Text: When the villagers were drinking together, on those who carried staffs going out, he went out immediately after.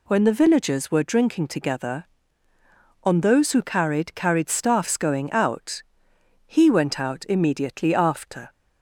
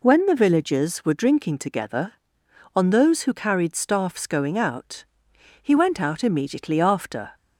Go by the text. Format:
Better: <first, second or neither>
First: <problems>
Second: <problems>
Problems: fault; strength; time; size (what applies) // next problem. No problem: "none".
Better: second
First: says "carried" twice; at 4.1 s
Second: none